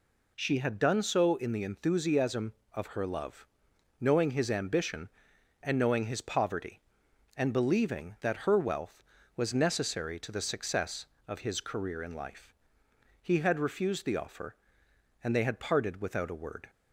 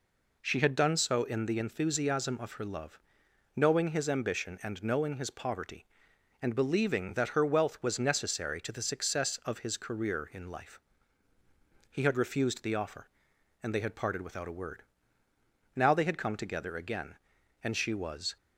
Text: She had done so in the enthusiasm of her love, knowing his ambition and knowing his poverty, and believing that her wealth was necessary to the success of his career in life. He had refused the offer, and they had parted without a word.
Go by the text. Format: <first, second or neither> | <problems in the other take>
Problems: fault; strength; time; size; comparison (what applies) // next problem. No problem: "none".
first | goes on to say "Now they had come together again and she was"; strong; from 15.7 s on; 2.6 s long